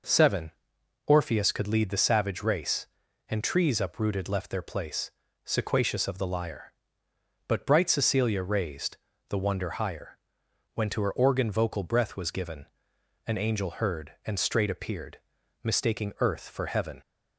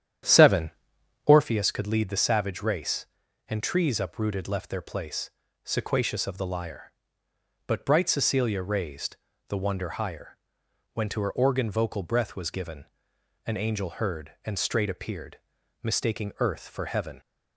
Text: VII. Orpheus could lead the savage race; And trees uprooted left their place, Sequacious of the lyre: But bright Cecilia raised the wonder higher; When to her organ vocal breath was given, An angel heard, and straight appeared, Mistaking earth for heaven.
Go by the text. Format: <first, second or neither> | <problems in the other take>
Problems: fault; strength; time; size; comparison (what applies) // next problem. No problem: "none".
first | starts louder than the rest; strong; until 1.5 s; 10 dB // pauses between "raised" and "the"; slight; at 9.1 s; 0.30 s long; slight in the first